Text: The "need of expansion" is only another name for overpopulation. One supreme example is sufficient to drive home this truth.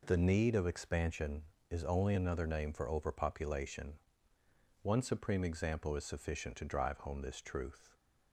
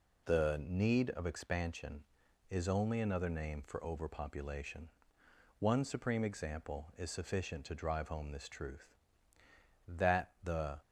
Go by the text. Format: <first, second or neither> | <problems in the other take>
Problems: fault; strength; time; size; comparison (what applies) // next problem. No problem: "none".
first | goes on to say "That the"; noticeable; from 9.8 s on; 0.94 s long